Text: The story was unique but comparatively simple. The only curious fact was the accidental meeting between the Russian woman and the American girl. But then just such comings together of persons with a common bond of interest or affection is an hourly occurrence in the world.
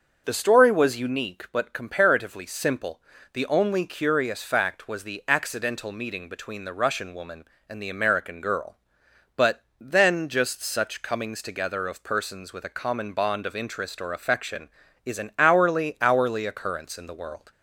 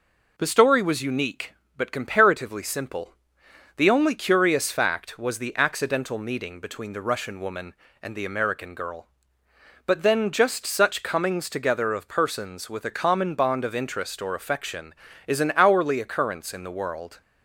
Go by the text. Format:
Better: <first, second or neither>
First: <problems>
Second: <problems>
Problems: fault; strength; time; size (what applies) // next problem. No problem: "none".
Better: second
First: pauses between "But" and "then"; slight; at 9.6 s; 0.18 s long // says "hourly" twice; at 16.0 s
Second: none